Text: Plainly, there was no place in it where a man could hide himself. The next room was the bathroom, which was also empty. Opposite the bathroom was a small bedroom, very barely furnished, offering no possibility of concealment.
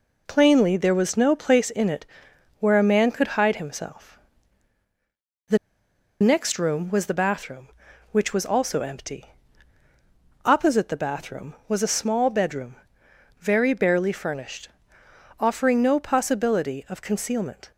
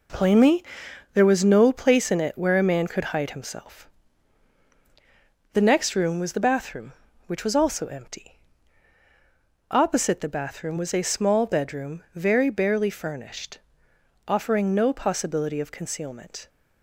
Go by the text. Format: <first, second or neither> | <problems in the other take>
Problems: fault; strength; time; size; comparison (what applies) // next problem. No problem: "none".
second | pauses between "it" and "where"; noticeable; at 2.0 s; 0.54 s long // pauses between "The" and "next"; noticeable; at 5.5 s; 0.63 s long